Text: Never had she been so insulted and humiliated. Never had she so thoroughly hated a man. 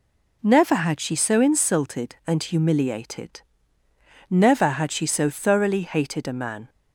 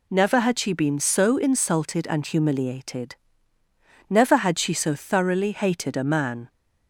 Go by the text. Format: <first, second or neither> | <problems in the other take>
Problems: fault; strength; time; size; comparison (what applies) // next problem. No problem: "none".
second | skips "been"; at 1.1 s